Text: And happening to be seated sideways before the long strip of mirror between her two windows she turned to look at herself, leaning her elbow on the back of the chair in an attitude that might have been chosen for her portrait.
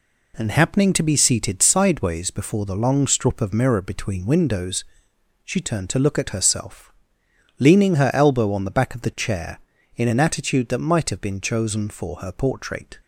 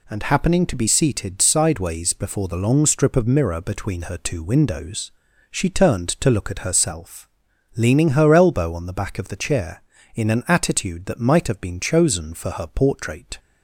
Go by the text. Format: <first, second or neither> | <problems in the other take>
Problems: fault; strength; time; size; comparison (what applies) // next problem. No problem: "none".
second | skips "her two"; at 4.2 s // pauses between "windows" and "she"; noticeable; at 4.8 s; 0.62 s long; also in the second